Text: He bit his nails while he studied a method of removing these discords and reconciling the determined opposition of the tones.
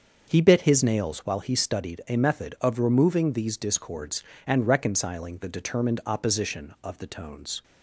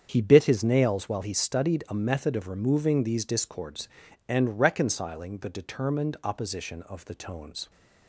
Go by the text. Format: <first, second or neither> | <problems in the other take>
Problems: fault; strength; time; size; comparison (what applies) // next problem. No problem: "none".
neither | starts louder than the rest; the same in both